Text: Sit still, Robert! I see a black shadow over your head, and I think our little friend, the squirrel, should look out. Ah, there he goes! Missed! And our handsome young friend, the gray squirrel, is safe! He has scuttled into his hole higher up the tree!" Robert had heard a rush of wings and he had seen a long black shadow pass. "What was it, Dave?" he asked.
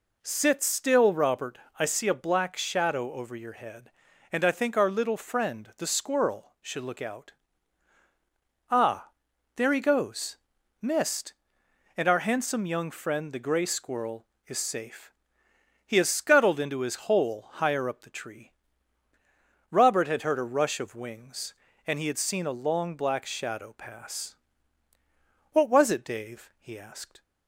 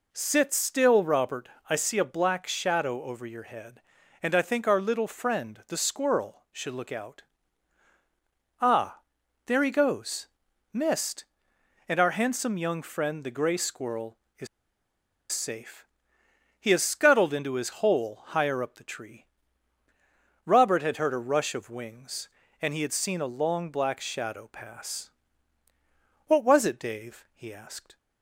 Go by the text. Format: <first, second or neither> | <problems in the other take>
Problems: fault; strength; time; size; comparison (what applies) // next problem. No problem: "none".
first | pauses between "is" and "safe"; noticeable; at 14.4 s; 0.85 s long